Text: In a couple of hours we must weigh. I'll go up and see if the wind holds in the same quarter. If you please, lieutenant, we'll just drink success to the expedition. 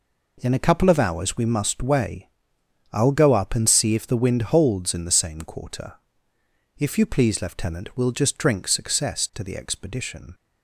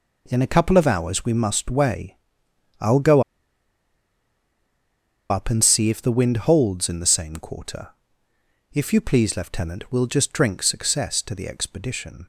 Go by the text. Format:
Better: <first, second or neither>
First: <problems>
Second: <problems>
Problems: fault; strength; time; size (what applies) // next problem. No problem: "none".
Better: first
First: none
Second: pauses between "go" and "up"; strong; at 3.2 s; 2.0 s long